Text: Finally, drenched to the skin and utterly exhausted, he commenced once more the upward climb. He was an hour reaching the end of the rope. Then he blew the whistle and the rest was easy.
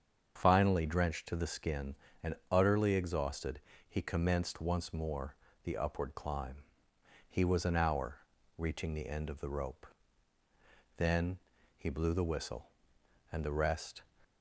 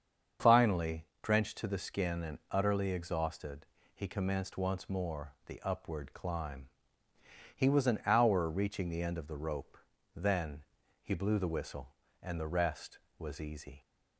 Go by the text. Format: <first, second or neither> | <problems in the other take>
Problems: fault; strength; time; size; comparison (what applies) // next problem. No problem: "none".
second | starts louder than the rest; strong; until 1.3 s; 7 dB; also in the second // pauses between "and" and "utterly"; slight; at 2.3 s; 0.16 s long // pauses between "more" and "the"; slight; at 5.3 s; 0.30 s long // pauses between "hour" and "reaching"; at 8.1 s; 0.40 s long // pauses between "Then" and "he"; at 11.3 s; 0.40 s long; also in the second // stops before "was easy"; at 14.2 s